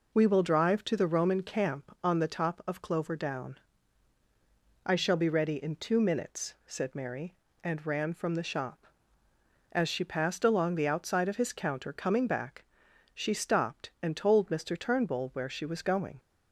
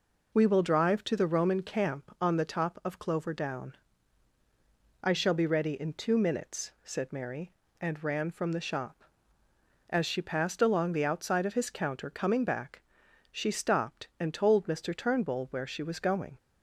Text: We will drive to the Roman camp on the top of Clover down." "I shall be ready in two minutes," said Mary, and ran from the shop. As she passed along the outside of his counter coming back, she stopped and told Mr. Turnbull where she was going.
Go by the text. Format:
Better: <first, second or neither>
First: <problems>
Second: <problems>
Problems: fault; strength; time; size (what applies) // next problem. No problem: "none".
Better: neither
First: none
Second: none